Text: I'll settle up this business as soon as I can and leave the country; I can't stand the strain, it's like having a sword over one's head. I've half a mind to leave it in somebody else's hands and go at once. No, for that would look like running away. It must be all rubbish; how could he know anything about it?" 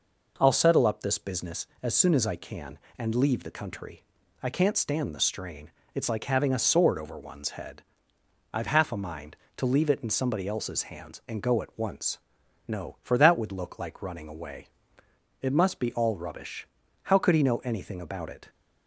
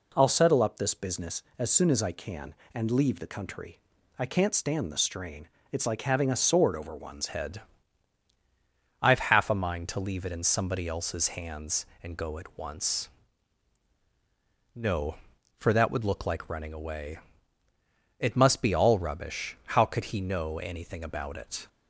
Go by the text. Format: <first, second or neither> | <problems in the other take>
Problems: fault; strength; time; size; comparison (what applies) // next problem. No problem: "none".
first | changes voice at "head"; from 7.2 s on; 14.4 s long